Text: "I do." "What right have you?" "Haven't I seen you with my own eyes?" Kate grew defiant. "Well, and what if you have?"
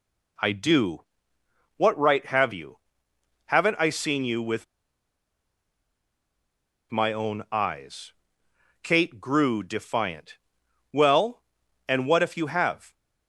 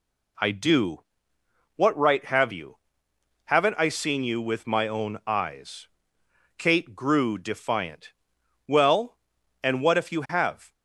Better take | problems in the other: second | pauses between "with" and "my"; strong; at 4.6 s; 2.2 s long

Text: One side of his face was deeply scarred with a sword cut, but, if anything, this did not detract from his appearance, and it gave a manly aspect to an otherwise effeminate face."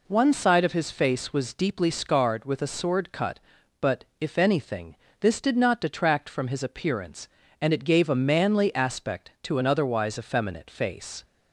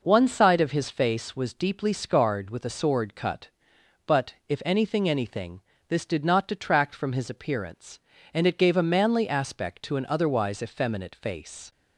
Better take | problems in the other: first | says "anything" twice; at 5.0 s

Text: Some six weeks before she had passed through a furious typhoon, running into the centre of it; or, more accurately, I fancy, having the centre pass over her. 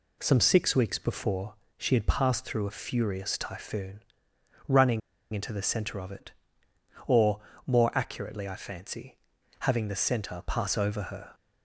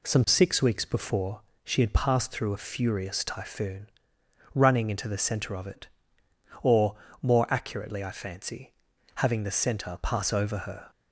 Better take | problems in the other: second | pauses between "before" and "she"; slight; at 1.5 s; 0.24 s long; slight in the second // pauses between "running" and "into"; slight; at 5.0 s; 0.32 s long

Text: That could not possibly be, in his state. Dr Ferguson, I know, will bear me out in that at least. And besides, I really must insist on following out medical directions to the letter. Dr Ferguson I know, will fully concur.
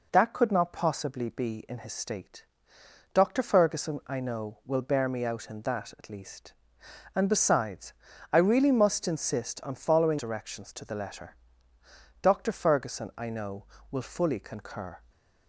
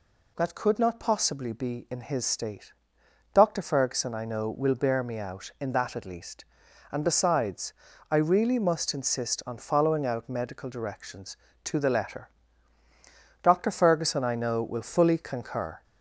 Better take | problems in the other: second | skips "out medical"; at 10.1 s

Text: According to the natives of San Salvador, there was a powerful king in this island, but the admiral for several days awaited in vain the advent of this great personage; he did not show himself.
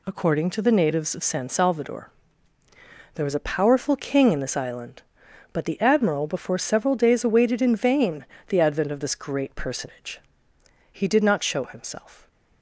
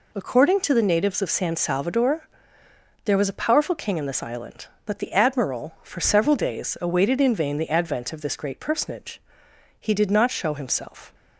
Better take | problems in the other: second | says "before" for "for"; at 6.2 s // pauses between "vain" and "the"; slight; at 8.2 s; 0.24 s long

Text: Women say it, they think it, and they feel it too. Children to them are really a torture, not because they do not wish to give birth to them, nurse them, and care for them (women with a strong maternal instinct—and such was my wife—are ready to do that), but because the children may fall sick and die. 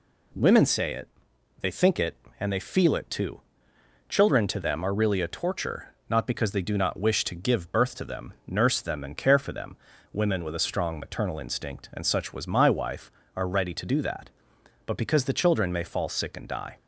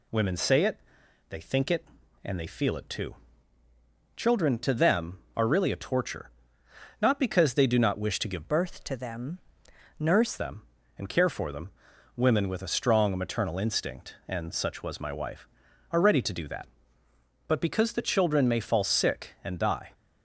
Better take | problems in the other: first | changes voice from "birth" to "nurse"; from 8.4 to 10.3 s; 1.9 s long

